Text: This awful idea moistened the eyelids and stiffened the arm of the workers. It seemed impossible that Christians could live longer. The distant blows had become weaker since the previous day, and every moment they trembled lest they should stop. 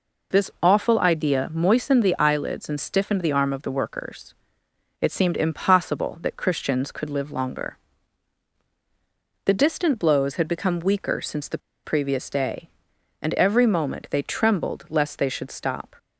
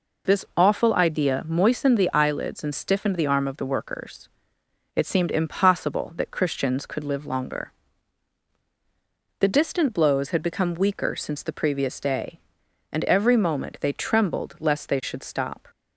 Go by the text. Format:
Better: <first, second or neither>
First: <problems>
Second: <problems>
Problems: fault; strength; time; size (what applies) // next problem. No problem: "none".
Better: second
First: pauses between "the" and "previous"; slight; at 11.5 s; 0.27 s long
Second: none